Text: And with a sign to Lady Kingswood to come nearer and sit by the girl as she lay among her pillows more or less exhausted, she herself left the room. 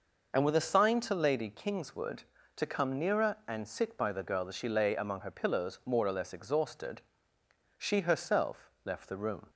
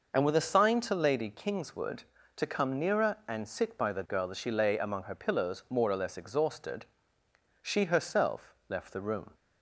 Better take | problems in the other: neither | none

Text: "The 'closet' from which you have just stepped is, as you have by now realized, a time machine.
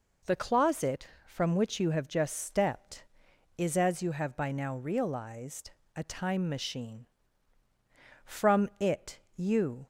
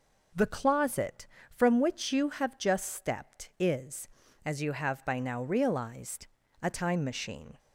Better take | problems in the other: second | goes on to say "From it you"; from 8.2 s on; 1.6 s long

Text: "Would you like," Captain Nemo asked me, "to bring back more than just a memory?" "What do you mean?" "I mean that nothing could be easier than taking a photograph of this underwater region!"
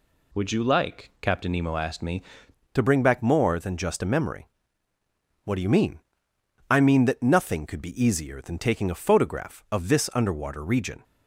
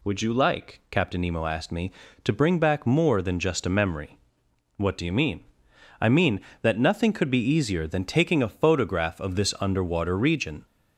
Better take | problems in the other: second | changes voice at "to"; from 2.7 s on; 8.3 s long

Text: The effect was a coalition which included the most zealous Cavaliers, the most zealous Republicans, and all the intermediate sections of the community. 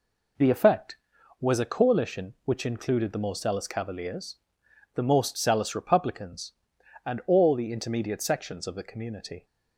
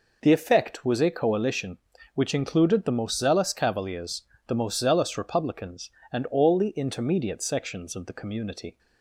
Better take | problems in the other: neither | none

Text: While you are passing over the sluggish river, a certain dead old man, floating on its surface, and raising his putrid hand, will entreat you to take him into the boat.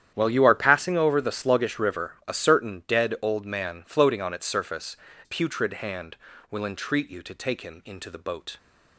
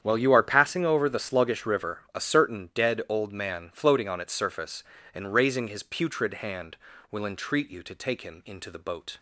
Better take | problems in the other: second | starts louder than the rest; strong; until 1.1 s; 10 dB; strong in the second // skips "and raising his"; at 5.0 s

